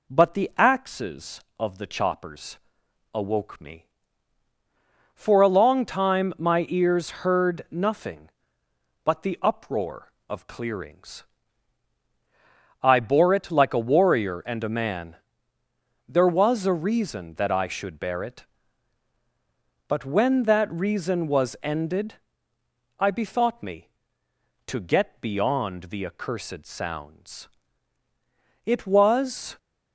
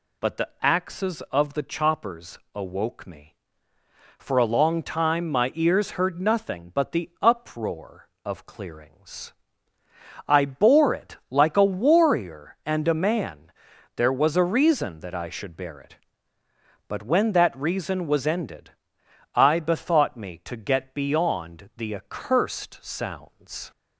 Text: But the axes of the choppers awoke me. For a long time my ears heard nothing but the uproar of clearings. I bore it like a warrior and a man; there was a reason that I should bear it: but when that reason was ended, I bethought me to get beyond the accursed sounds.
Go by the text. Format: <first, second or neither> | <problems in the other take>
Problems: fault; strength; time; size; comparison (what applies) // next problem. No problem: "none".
second | pauses between "choppers" and "awoke"; noticeable; at 2.5 s; 0.56 s long; slight in the second // goes on to say "It was"; noticeable; from 28.6 s on; 0.94 s long